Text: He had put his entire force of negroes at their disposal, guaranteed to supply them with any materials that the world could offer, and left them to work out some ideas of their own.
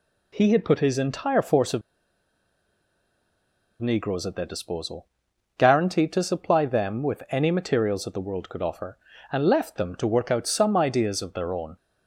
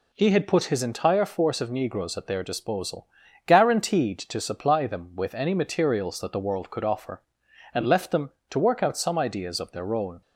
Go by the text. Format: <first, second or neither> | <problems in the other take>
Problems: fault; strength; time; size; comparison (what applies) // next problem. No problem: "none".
second | pauses between "of" and "negroes"; strong; at 1.8 s; 2.0 s long